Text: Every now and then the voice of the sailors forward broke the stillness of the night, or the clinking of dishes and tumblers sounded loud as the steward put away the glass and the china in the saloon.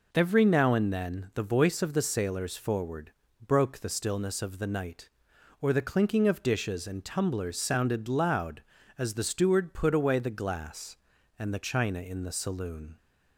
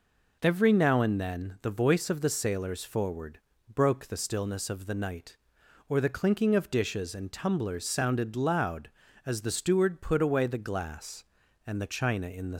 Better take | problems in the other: first | pauses between "forward" and "broke"; slight; at 3.4 s; 0.34 s long; slight in the first // stops before "saloon"; at 12.5 s

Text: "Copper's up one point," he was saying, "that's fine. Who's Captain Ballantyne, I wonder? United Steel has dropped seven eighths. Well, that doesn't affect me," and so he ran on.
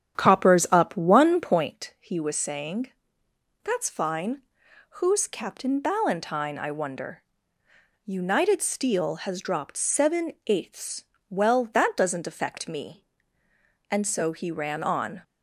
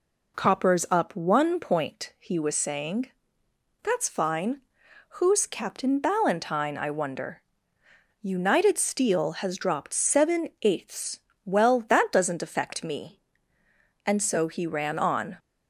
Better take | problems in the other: second | starts louder than the rest; strong; until 1.8 s; 9.5 dB

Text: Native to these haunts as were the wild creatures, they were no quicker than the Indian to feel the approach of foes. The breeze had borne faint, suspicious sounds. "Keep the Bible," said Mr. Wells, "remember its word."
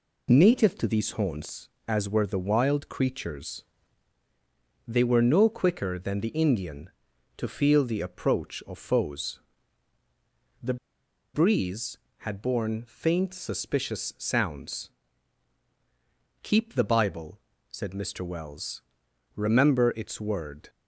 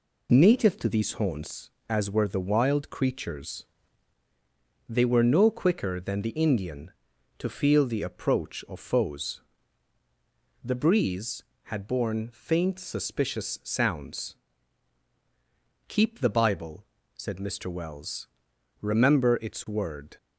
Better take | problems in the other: second | pauses between "The" and "breeze"; noticeable; at 10.7 s; 0.58 s long

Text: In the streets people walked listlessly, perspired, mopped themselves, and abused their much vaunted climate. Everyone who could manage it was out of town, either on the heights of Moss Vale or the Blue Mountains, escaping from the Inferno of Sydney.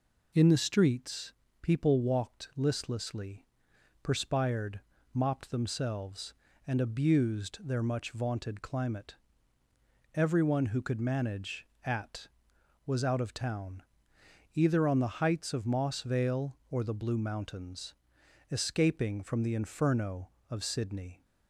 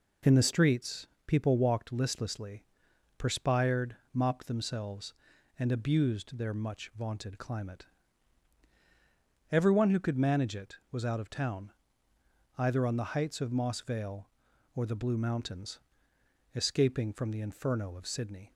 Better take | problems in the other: second | pauses between "streets" and "people"; slight; at 1.3 s; 0.26 s long; slight in the second // says "at" for "it"; at 11.8 s

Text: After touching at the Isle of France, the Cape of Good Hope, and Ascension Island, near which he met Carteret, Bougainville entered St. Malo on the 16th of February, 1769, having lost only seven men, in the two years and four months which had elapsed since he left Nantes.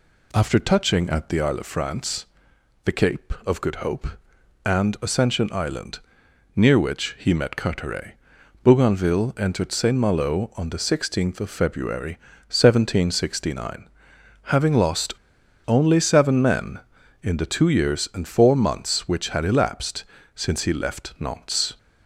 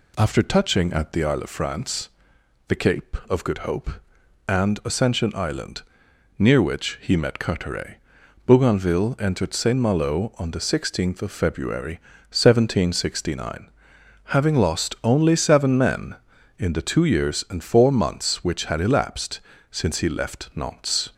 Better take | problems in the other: second | pauses between "lost" and "only"; noticeable; at 15.1 s; 0.53 s long // pauses between "elapsed" and "since"; slight; at 20.0 s; 0.32 s long; slight in the second

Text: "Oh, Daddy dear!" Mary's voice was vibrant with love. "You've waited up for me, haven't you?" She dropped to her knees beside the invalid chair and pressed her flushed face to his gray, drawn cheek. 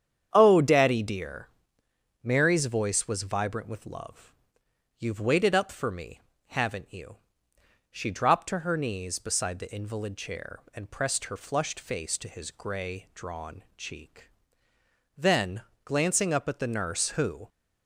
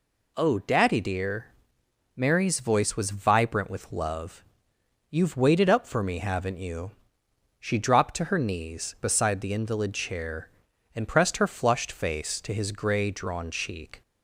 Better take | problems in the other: second | starts louder than the rest; strong; until 1.3 s; 8.5 dB // goes on to say "Then glancing up at the nurse who"; strong; from 15.1 s on; 2.3 s long

